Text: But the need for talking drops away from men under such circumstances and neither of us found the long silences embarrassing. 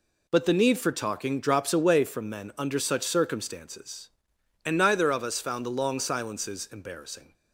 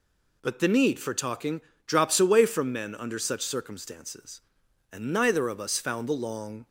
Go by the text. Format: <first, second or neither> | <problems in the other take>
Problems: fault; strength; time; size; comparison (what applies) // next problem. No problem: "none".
first | pauses between "talking" and "drops"; slight; at 1.6 s; 0.24 s long // stops before "silences embarrassing"; at 6.6 s